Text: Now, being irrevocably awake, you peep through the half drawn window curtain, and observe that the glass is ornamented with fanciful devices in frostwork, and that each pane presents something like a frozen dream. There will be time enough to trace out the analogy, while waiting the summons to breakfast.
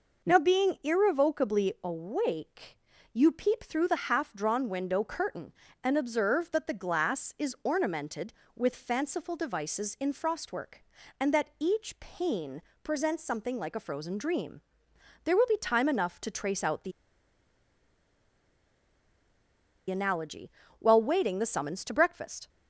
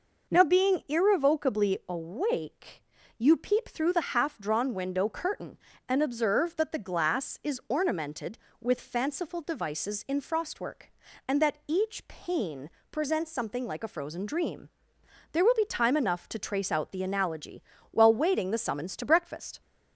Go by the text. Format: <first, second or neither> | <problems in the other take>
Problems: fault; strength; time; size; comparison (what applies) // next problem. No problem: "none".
second | pauses between "pane" and "presents"; slight; at 12.6 s; 0.20 s long; slight in the second // pauses between "the" and "analogy"; strong; at 16.9 s; 2.9 s long